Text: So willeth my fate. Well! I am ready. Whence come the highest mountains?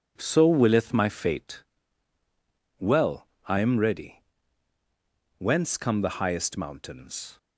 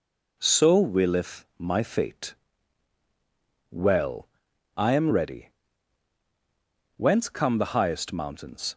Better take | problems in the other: neither | none

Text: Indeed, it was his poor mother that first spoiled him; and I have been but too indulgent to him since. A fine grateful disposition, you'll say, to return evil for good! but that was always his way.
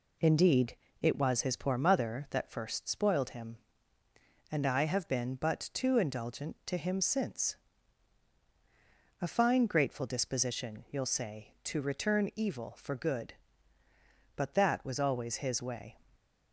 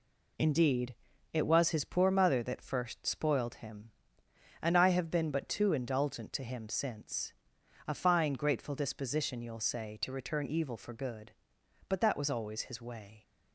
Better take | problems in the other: neither | none

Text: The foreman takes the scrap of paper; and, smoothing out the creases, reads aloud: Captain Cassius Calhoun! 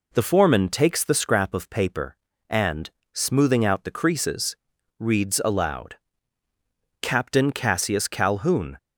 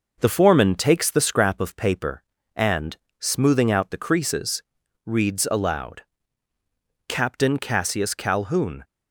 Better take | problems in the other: first | gets quieter; slight; throughout; 2.5 dB

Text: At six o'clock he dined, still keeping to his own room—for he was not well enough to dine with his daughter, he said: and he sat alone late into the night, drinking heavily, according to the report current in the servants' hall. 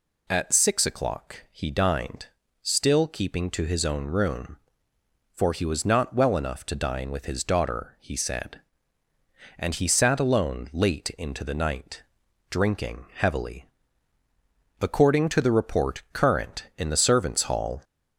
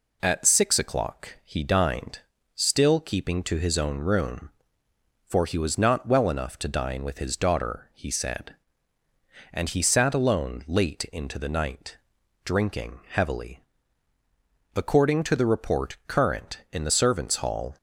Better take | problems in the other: second | gets louder; slight; throughout; 2 dB

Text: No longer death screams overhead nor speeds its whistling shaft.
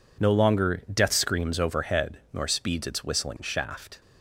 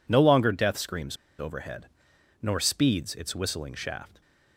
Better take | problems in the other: first | pauses between "screams" and "overhead"; slight; at 1.1 s; 0.22 s long // pauses between "overhead" and "nor"; noticeable; at 1.8 s; 0.54 s long; slight in the first

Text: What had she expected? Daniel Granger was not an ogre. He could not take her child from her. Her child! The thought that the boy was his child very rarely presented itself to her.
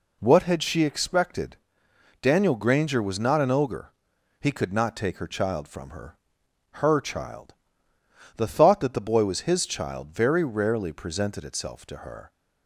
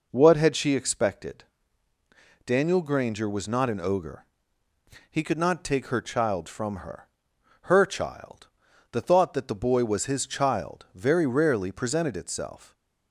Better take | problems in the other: first | stops before "to her"; at 12.7 s

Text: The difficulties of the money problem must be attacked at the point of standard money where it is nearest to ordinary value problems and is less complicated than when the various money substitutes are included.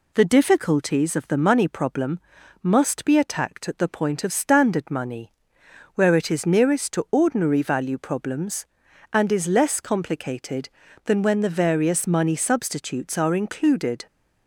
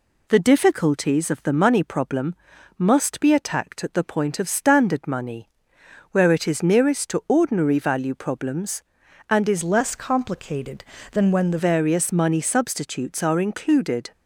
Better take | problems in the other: first | pauses between "problem" and "must"; noticeable; at 2.3 s; 0.46 s long; noticeable in the first // pauses between "money" and "where"; noticeable; at 5.4 s; 0.64 s long; noticeable in the first // changes voice from "less" to "the"; from 9.6 to 11.5 s; 1.9 s long

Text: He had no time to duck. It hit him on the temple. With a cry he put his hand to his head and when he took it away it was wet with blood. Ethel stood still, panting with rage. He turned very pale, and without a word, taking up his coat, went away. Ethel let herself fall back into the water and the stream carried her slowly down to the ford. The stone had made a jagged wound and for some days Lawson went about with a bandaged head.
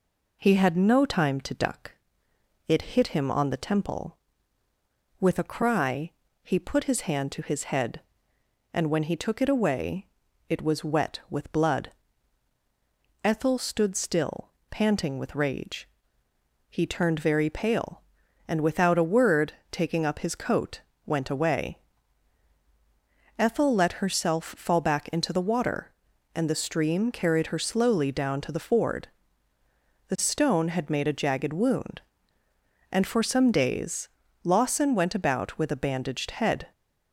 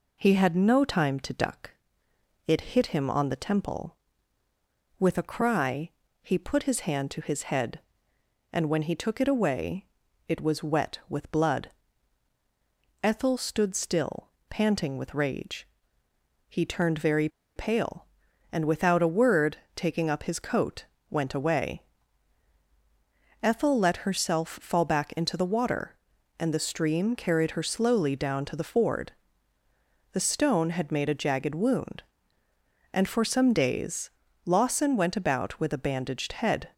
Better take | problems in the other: first | pauses between "cry" and "he"; slight; at 5.8 s; 0.34 s long; slight in the first // pauses between "away" and "it"; at 9.8 s; 0.42 s long; also in the first // pauses between "very" and "pale"; slight; at 17.2 s; 0.28 s long // pauses between "days" and "Lawson"; slight; at 34.1 s; 0.34 s long; slight in the first

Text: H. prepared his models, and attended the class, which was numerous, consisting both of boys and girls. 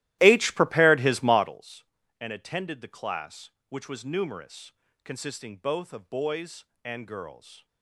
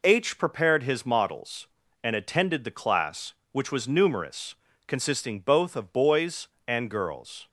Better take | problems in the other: second | starts louder than the rest; strong; until 1.6 s; 15.5 dB

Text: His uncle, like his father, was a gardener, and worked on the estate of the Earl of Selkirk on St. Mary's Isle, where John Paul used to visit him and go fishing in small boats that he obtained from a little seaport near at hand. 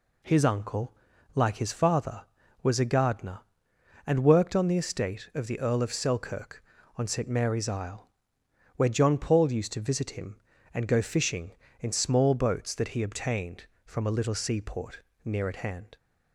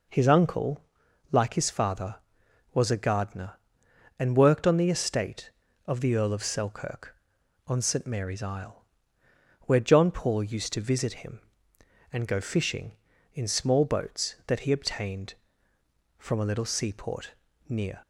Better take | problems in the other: first | pauses between "seaport" and "near"; slight; at 17.3 s; 0.32 s long; slight in the first // stops before "at hand"; at 18.0 s

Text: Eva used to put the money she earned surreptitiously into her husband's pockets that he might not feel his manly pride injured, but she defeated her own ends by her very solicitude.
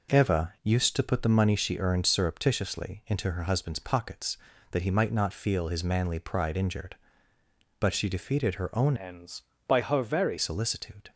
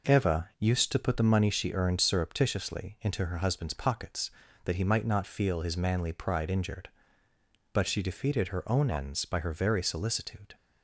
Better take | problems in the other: second | changes voice from "ends" to "very"; from 8.9 to 10.3 s; 1.4 s long

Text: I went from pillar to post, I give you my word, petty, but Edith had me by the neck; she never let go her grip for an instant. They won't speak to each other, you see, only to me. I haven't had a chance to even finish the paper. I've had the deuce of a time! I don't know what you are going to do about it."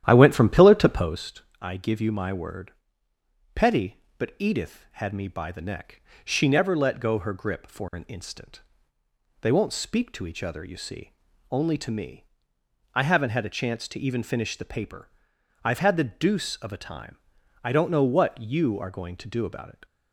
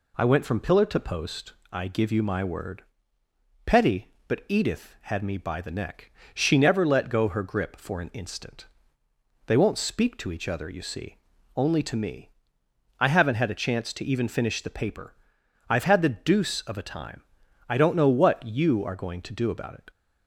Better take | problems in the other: second | starts louder than the rest; strong; until 1.3 s; 11 dB

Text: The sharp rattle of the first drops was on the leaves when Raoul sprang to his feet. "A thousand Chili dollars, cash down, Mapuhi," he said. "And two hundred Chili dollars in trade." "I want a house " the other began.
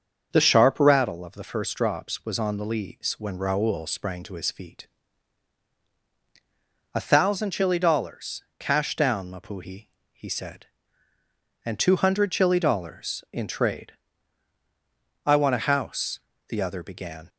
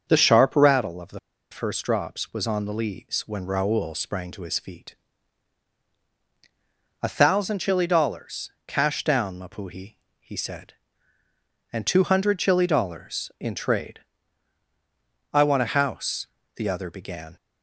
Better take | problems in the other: first | starts louder than the rest; until 1.0 s; 6.5 dB; also in the first // pauses between "the" and "first"; slight; at 1.1 s; 0.32 s long

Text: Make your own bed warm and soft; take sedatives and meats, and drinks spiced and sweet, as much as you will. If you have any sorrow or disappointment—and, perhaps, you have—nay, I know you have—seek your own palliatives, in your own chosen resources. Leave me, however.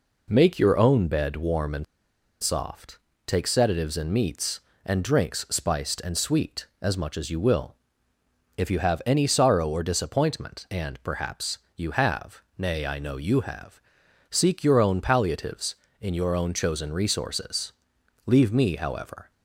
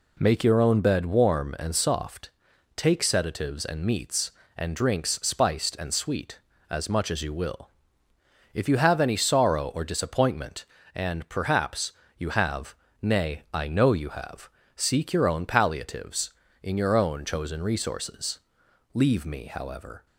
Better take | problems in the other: second | pauses between "and" and "soft"; noticeable; at 1.8 s; 0.57 s long

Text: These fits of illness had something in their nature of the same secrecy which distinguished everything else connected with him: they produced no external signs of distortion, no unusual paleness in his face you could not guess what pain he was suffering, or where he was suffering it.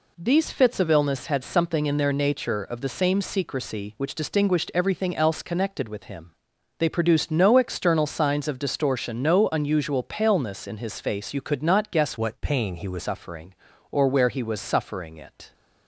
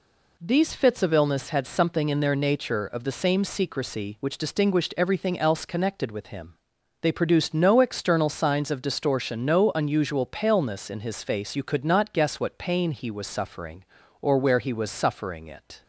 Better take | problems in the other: second | changes voice from "what" to "was"; from 12.1 to 13.0 s; 0.9 s long

